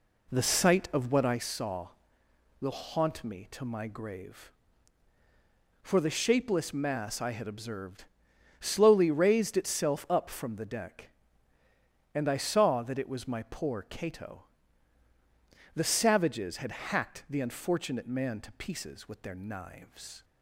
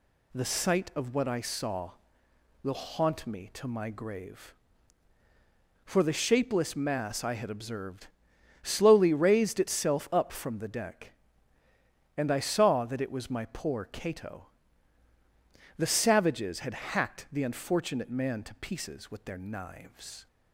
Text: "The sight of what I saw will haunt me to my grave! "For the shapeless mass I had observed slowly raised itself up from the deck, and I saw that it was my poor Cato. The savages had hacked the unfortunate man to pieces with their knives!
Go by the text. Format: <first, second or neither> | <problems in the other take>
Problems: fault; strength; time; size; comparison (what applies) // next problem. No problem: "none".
second | starts louder than the rest; slight; until 1.4 s; 3 dB // pauses between "observed" and "slowly"; noticeable; at 8.0 s; 0.56 s long; noticeable in the second